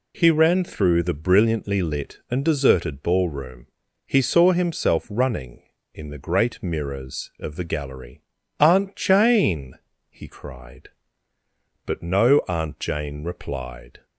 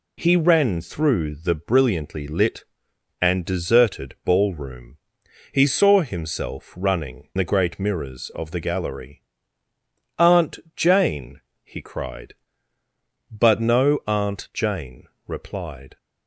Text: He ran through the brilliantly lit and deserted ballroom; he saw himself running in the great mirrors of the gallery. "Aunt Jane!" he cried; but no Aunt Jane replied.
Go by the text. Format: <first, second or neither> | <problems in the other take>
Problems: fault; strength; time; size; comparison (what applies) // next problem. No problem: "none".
first | skips "in"; at 7.3 s // pauses between "Aunt" and "Jane"; slight; at 10.5 s; 0.18 s long // pauses between "Jane" and "replied"; slight; at 15.0 s; 0.20 s long